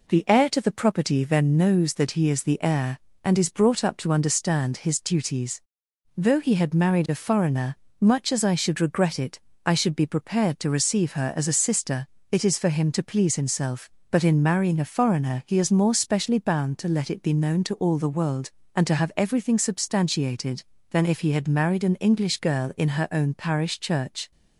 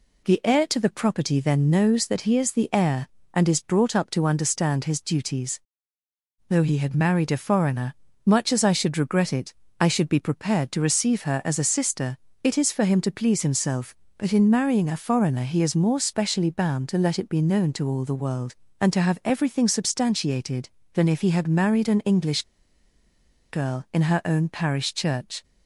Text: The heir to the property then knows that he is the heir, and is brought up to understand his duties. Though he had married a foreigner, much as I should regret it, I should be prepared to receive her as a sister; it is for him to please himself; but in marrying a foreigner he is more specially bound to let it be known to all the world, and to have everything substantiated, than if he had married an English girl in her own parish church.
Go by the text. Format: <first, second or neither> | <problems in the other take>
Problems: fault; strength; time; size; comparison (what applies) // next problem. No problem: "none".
first | pauses between "English" and "girl"; at 22.4 s; 1.0 s long